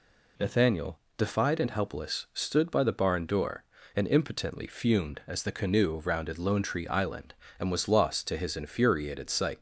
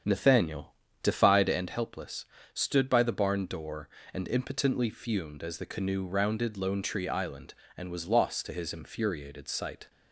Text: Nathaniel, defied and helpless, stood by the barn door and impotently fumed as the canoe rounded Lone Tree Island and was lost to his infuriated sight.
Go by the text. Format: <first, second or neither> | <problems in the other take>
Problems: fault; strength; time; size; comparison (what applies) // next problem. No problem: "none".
first | starts louder than the rest; strong; until 1.6 s; 7.5 dB